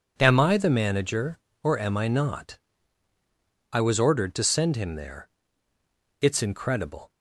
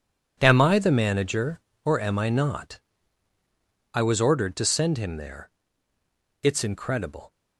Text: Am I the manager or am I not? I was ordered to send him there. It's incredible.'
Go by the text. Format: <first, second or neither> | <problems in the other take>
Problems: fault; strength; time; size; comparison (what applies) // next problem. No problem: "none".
first | gets quieter; strong; throughout; 12.5 dB